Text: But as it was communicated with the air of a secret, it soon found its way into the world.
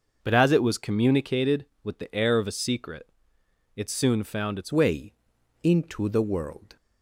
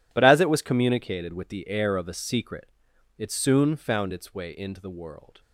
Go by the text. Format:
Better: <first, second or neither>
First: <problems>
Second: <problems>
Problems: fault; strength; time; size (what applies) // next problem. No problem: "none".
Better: second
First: starts louder than the rest; noticeable; until 1.2 s; 6 dB // changes voice at "way"; from 4.7 s on; 2.0 s long // pauses between "way" and "into"; noticeable; at 5.1 s; 0.50 s long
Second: none